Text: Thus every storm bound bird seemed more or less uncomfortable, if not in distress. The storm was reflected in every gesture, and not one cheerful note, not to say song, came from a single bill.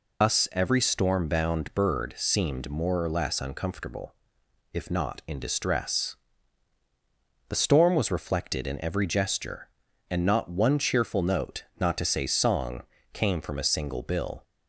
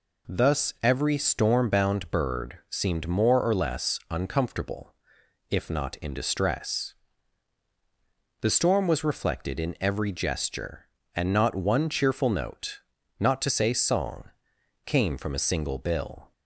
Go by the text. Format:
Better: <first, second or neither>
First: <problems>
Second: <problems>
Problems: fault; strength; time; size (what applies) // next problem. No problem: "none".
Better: second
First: loses the start of "Thus"; at 0.2 s; 170 ms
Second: none